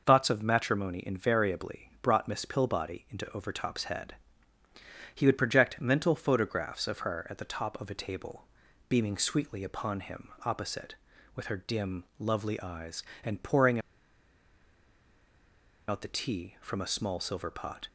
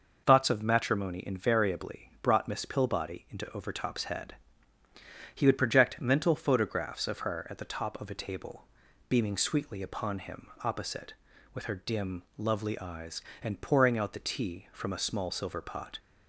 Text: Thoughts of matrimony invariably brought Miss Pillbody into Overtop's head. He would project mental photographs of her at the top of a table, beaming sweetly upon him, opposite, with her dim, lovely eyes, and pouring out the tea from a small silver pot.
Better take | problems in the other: second | pauses between "pouring" and "out"; strong; at 13.7 s; 2.0 s long

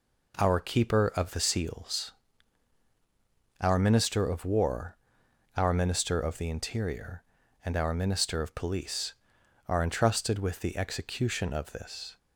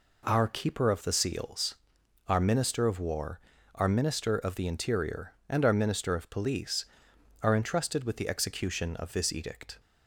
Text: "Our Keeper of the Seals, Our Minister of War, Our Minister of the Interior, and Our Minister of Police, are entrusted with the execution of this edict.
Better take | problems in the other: second | stops before "edict"; at 12.1 s

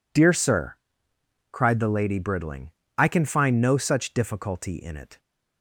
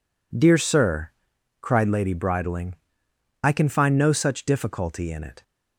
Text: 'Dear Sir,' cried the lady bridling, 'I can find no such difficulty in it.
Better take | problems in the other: first | skips "the"; at 1.8 s

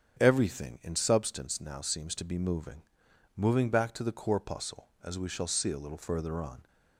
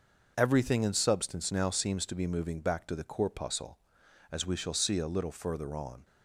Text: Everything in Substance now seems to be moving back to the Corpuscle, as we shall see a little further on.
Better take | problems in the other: second | starts louder than the rest; strong; until 1.2 s; 8.5 dB // says "moving" twice; at 3.3 s

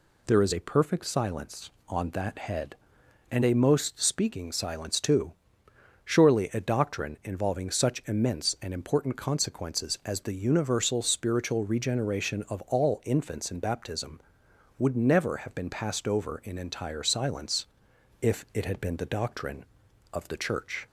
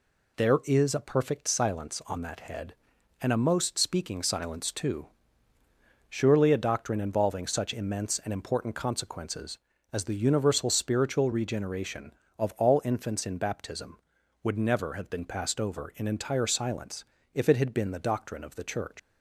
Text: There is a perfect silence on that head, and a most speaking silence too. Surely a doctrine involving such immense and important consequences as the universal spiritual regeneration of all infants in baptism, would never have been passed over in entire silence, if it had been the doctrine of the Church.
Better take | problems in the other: first | leaves "Church" unfinished; at 18.9 s; 130 ms

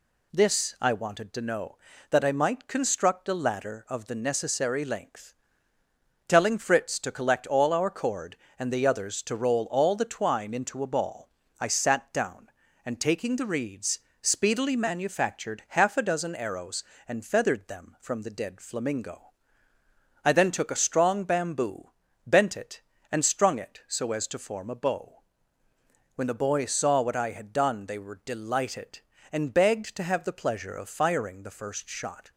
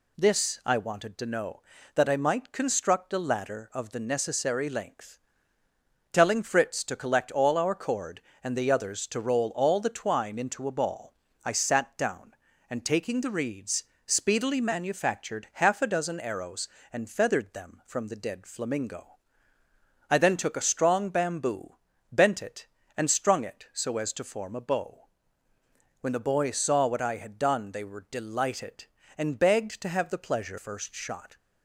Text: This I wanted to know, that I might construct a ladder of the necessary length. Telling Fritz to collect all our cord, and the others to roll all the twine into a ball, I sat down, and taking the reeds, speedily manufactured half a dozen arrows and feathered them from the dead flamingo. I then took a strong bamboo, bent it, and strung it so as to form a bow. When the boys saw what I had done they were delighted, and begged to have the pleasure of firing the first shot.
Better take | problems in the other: first | skips "of firing the"; at 30.5 s

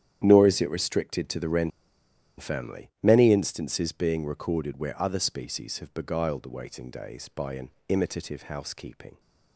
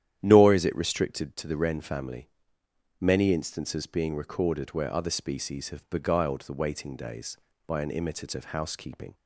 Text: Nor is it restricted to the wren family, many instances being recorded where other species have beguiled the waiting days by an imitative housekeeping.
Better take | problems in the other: second | starts louder than the rest; strong; until 1.2 s; 10 dB; strong in the second // pauses between "wren" and "family"; noticeable; at 1.7 s; 0.69 s long // pauses between "an" and "imitative"; slight; at 7.6 s; 0.18 s long

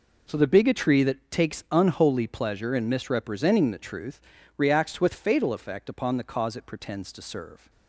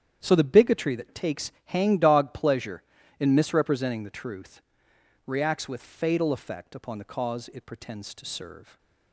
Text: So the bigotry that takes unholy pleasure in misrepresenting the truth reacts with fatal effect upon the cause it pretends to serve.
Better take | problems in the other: first | starts louder than the rest; strong; until 1.2 s; 9 dB // says "hangdog" for "unholy"; at 1.7 s // pauses between "truth" and "reacts"; noticeable; at 4.6 s; 0.64 s long; also in the first

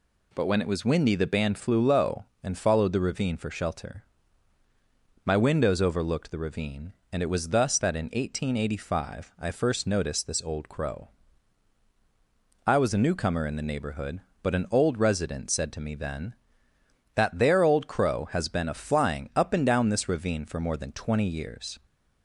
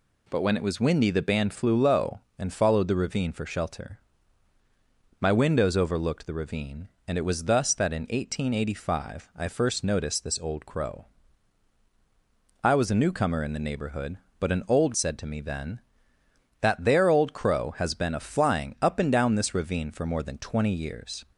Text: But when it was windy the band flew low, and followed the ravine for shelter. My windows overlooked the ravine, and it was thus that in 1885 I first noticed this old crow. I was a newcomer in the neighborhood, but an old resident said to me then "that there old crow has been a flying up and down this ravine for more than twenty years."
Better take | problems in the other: first | skips "resident"; at 14.9 s

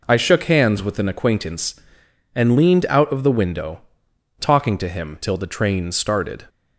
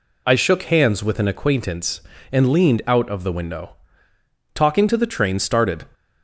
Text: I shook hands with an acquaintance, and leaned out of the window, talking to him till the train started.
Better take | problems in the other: first | skips "him till"; at 4.9 s

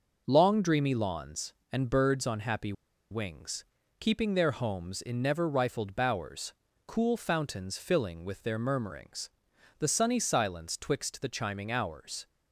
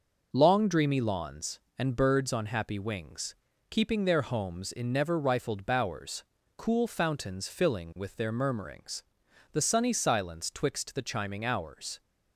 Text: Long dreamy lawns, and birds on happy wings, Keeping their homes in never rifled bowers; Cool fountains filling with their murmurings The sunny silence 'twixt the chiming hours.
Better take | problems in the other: second | pauses between "happy" and "wings"; at 2.7 s; 0.37 s long // pauses between "murmurings" and "The"; noticeable; at 9.3 s; 0.48 s long; noticeable in the second

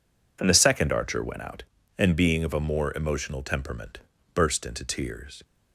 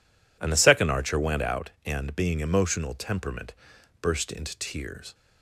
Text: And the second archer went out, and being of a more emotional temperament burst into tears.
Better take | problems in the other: first | skips "of a more"; at 2.3 s // pauses between "temperament" and "burst"; noticeable; at 3.5 s; 0.46 s long; slight in the first

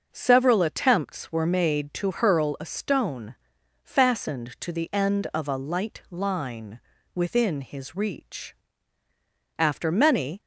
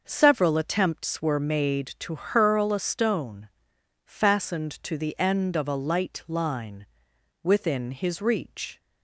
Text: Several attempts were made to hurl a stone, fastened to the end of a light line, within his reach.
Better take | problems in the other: second | starts louder than the rest; noticeable; until 1.1 s; 6 dB; noticeable in the second // goes on to say "After many"; noticeable; from 9.5 s on; 0.82 s long

